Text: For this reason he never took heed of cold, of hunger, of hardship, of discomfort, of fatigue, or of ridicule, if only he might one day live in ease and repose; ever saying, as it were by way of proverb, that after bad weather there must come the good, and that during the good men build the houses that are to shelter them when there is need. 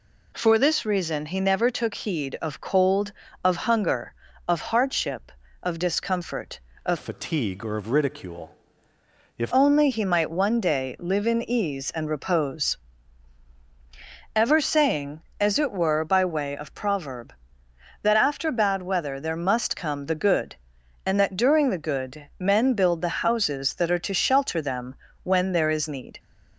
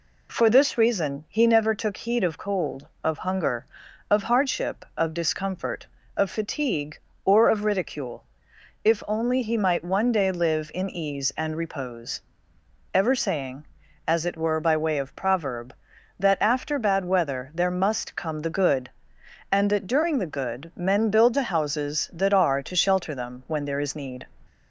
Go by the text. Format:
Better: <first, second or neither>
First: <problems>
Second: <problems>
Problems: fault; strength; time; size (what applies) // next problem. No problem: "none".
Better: second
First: changes voice from "fatigue" to "if"; from 6.9 to 9.5 s; 2.6 s long // pauses between "them" and "when"; slight; at 24.9 s; 0.30 s long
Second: none